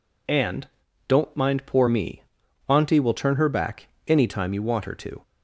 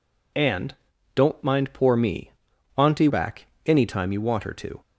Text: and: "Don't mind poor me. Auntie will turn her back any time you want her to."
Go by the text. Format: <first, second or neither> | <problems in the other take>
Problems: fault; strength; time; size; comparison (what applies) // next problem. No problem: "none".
first | skips "will turn her"; at 3.0 s // pauses between "back" and "any"; slight; at 3.4 s; 0.18 s long; slight in the first